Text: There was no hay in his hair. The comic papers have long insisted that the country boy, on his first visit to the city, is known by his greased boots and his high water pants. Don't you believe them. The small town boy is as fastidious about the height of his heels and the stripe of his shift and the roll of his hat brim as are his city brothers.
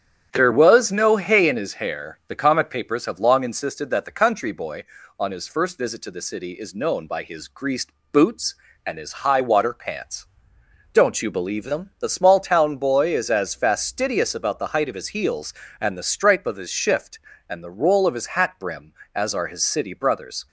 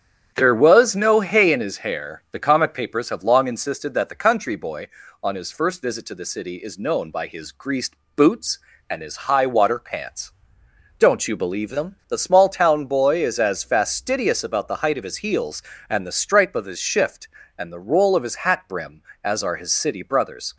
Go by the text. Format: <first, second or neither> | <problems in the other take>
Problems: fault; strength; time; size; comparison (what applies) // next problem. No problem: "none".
neither | starts louder than the rest; strong; the same in both // pauses between "greased" and "boots"; slight; the same in both